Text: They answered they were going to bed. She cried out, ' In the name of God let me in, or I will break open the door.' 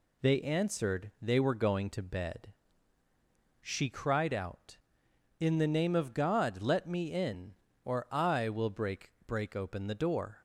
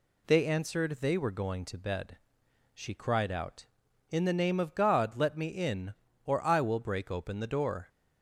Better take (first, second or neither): second